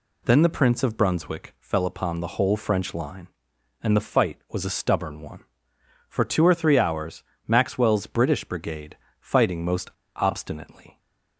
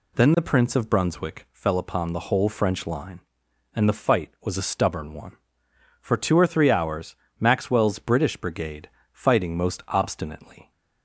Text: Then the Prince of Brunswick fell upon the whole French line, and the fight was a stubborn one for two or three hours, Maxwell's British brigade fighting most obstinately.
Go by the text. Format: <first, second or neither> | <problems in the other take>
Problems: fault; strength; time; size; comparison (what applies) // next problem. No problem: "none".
second | pauses between "brigade" and "fighting"; slight; at 8.9 s; 0.20 s long; slight in the second // pauses between "most" and "obstinately"; slight; at 9.8 s; 0.26 s long